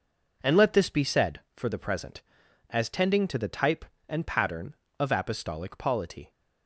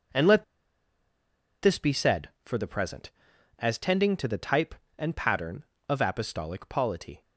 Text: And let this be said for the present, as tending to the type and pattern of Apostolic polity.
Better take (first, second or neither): first